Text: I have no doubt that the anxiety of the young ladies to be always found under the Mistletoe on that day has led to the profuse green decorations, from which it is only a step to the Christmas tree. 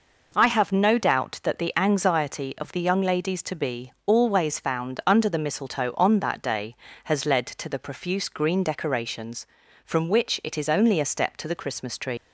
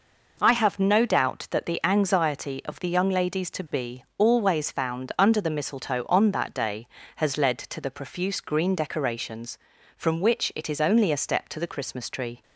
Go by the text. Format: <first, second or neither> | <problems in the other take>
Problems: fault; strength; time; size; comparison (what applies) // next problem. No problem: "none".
second | pauses between "be" and "always"; slight; at 3.9 s; 0.16 s long; slight in the second // leaves "tree" unfinished; at 12.1 s; 130 ms